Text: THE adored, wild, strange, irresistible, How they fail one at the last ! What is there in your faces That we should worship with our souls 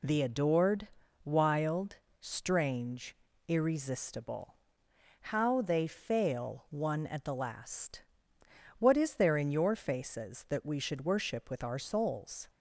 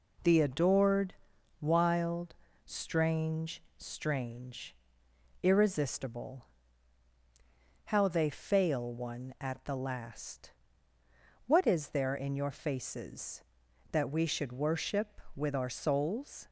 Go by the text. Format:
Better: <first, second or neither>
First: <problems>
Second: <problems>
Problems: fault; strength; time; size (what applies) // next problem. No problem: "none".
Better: first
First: none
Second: says "strange" twice; at 3.8 s